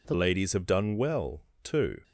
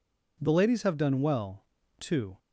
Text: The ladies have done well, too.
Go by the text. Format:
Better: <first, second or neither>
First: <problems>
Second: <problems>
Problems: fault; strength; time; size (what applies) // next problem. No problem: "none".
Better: second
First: changes voice at "ladies"; from 0.1 s on; 1.9 s long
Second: none